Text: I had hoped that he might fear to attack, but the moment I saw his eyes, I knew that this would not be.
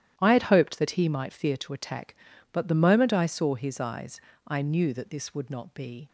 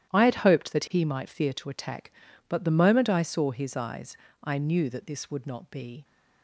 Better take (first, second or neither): neither